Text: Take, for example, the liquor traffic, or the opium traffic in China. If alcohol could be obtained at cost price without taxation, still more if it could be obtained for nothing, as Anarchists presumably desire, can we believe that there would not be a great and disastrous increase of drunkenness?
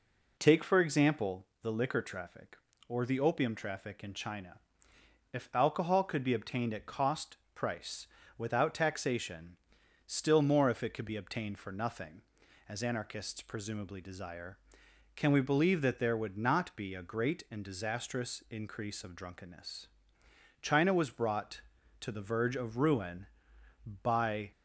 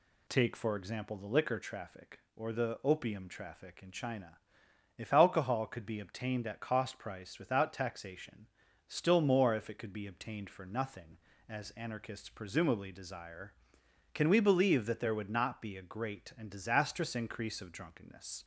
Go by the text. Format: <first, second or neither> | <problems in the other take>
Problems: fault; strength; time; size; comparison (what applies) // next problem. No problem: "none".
second | pauses between "cost" and "price"; slight; at 7.3 s; 0.18 s long // pauses between "price" and "without"; slight; at 8.0 s; 0.30 s long // goes on to say "China was brought to the verge of ruin by"; strong; from 20.6 s on; 3.9 s long